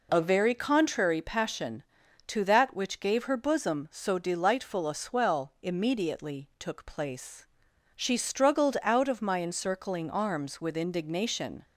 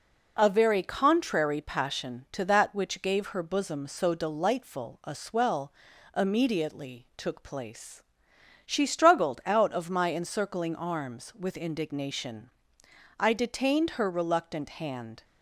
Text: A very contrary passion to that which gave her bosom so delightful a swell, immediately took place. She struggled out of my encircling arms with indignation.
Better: first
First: none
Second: goes on to say "I detained her reluctant hand"; strong; from 13.1 s on; 2.0 s long

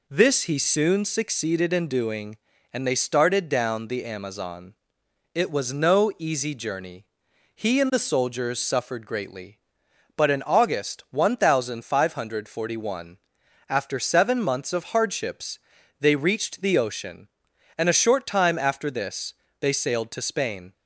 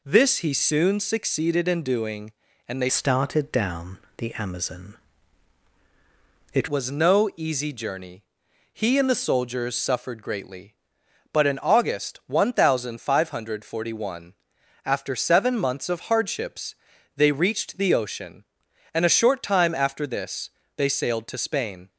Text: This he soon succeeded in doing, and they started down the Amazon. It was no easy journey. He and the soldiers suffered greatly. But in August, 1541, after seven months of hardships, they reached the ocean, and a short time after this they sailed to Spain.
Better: first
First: pauses between "this" and "they"; slight; at 19.3 s; 0.26 s long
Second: changes voice from "started" to "It"; from 2.8 to 6.6 s; 3.8 s long // pauses between "down" and "the"; slight; at 3.9 s; 0.18 s long // pauses between "this" and "they"; slight; at 20.5 s; 0.26 s long

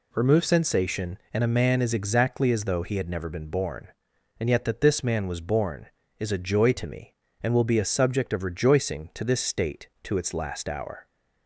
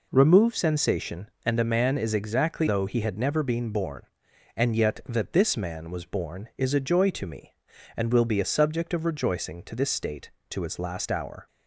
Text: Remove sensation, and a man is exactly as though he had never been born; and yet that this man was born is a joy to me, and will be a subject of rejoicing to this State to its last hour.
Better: first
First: none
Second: skips "as"; at 2.6 s

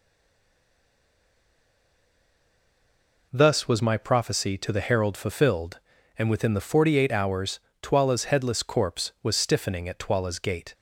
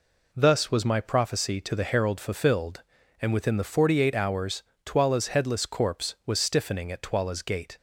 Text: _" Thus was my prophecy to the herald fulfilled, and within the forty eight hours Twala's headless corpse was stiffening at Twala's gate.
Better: second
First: stays silent before the first word; strong; until 3.2 s; 3.2 s long // pauses between "hours" and "Twala's"; slight; at 7.5 s; 0.20 s long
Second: pauses between "hours" and "Twala's"; slight; at 4.6 s; 0.20 s long

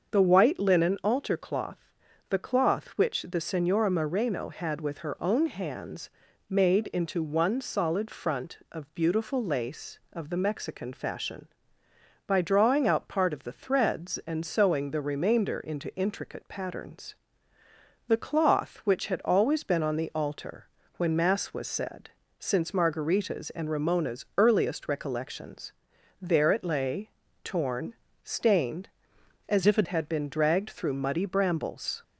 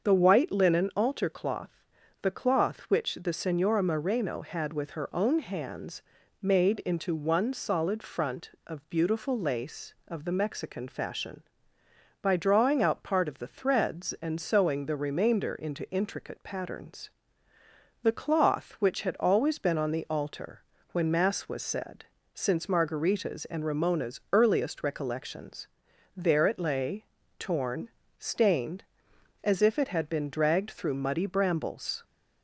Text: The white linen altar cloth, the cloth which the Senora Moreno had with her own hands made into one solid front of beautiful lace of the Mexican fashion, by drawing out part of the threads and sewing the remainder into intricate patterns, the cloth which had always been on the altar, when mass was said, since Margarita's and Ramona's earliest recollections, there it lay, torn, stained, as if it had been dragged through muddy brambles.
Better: second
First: starts louder than the rest; until 1.1 s; 6.5 dB // pauses between "hands" and "made"; at 6.1 s; 0.38 s long // changes voice from "if" to "it"; from 29.6 to 29.8 s; 0.2 s long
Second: starts louder than the rest; until 1.0 s; 6.5 dB // pauses between "hands" and "made"; at 6.0 s; 0.38 s long

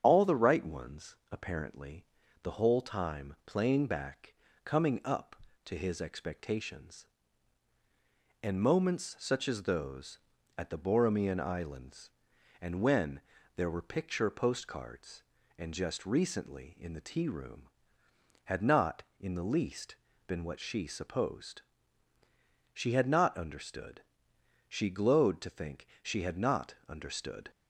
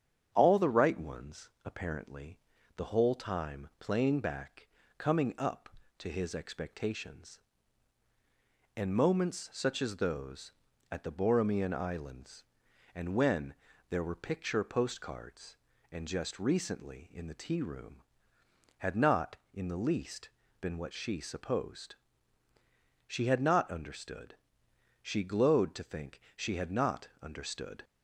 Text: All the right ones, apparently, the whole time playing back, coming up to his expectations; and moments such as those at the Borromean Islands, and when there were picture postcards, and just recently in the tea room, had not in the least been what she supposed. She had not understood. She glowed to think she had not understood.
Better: second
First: loses the start of "All"; at 0.0 s; 40 ms // starts louder than the rest; strong; until 1.0 s; 7.5 dB // pauses between "when" and "there"; slight; at 13.2 s; 0.36 s long // pauses between "least" and "been"; slight; at 19.9 s; 0.32 s long // pauses between "think" and "she"; slight; at 25.8 s; 0.16 s long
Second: starts louder than the rest; strong; until 1.3 s; 8 dB // pauses between "when" and "there"; slight; at 13.5 s; 0.36 s long // pauses between "least" and "been"; slight; at 20.2 s; 0.32 s long // pauses between "think" and "she"; slight; at 26.2 s; 0.16 s long

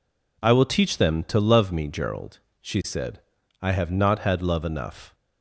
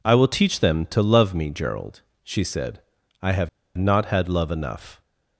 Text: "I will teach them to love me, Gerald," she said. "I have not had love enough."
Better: first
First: none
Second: pauses between "have" and "not"; slight; at 3.4 s; 0.27 s long

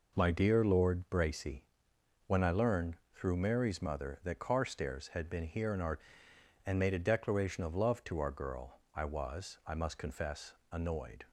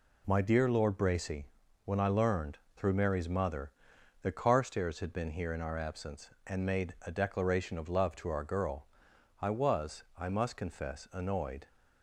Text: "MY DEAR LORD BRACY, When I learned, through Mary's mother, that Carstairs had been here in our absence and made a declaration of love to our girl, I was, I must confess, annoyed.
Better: second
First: skips "absence"; at 6.3 s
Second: none

